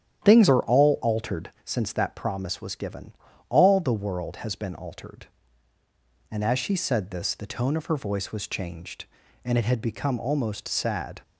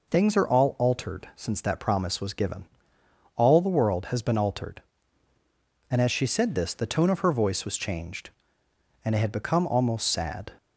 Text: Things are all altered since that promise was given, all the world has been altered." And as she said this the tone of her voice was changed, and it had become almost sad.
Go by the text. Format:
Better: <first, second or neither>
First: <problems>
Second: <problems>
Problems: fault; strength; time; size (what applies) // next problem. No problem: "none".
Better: second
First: starts louder than the rest; strong; until 1.7 s; 10 dB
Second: none